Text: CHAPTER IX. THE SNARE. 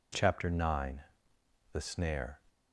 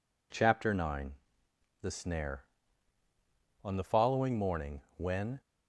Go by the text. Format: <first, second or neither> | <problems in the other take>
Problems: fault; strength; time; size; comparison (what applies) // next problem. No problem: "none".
first | goes on to say "On the following morning when"; strong; from 3.6 s on; 1.7 s long